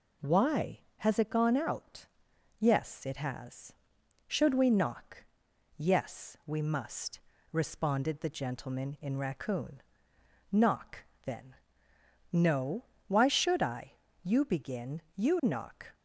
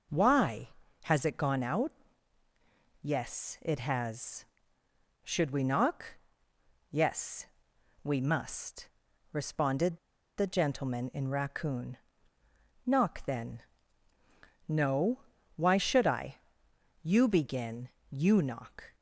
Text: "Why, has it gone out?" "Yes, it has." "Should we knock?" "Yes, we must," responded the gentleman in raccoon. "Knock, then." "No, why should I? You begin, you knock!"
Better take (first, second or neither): first